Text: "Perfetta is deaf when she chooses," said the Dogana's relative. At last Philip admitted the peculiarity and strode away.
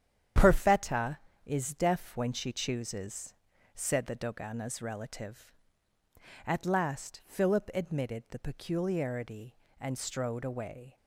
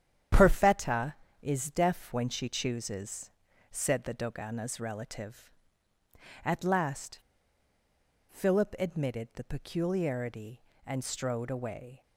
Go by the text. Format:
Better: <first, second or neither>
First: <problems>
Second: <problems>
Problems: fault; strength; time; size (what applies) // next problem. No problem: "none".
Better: first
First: starts louder than the rest; strong; until 1.6 s; 9 dB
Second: starts louder than the rest; strong; until 1.6 s; 9 dB // pauses between "last" and "Philip"; at 7.1 s; 1.0 s long